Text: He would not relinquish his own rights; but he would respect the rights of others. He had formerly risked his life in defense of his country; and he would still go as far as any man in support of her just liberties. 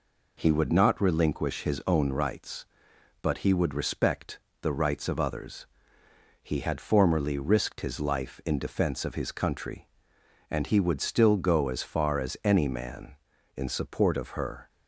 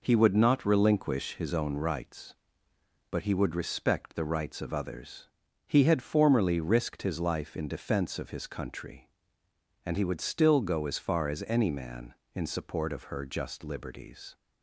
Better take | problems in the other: second | pauses between "respect" and "the"; slight; at 4.3 s; 0.22 s long // stops before "just liberties"; at 14.6 s

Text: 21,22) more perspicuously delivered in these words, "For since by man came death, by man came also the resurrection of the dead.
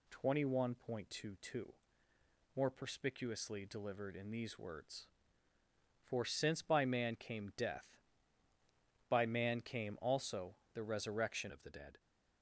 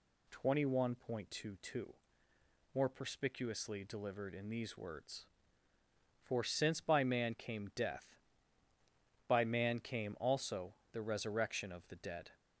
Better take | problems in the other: second | pauses between "also" and "the"; slight; at 10.5 s; 0.18 s long; slight in the second // changes voice at "of"; from 11.5 s on; 0.4 s long

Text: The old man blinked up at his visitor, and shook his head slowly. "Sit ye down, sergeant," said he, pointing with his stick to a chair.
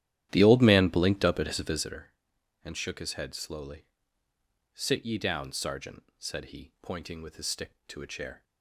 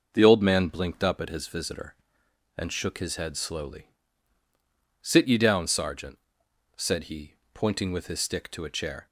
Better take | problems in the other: second | starts louder than the rest; strong; until 2.0 s; 12 dB

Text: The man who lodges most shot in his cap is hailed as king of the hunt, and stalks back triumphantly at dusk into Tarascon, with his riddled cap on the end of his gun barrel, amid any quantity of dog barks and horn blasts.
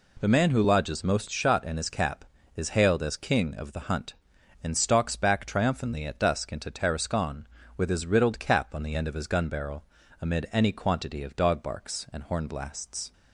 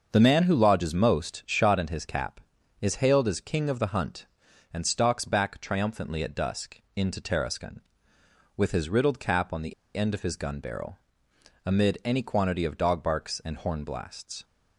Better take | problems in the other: first | starts louder than the rest; until 1.1 s; 6.5 dB // pauses between "dusk" and "into"; slight; at 6.8 s; 0.16 s long // pauses between "the" and "end"; slight; at 9.7 s; 0.22 s long

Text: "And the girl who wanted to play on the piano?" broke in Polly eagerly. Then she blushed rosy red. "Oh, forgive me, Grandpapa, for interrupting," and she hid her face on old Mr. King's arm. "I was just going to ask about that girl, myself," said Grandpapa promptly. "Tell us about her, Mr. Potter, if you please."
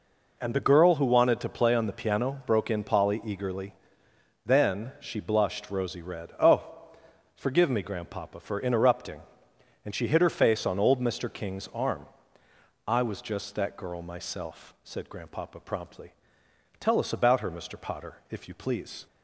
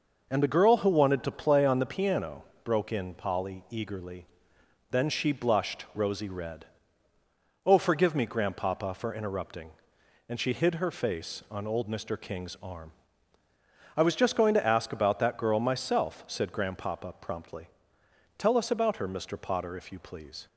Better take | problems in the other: second | skips "going to ask about"; at 13.5 s

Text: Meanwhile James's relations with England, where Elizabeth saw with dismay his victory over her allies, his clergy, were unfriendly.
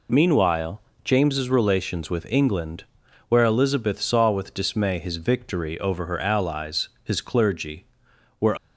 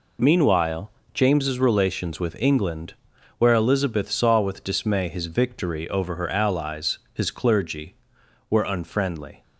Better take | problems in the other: second | pauses between "Meanwhile" and "James's"; slight; at 0.8 s; 0.24 s long; slight in the second // stops before "unfriendly"; at 8.5 s

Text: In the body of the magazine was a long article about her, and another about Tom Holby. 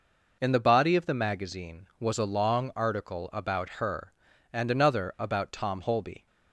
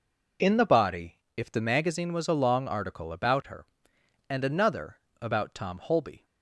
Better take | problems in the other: first | says "if" for "of"; at 1.3 s // pauses between "another" and "about"; slight; at 4.9 s; 0.24 s long

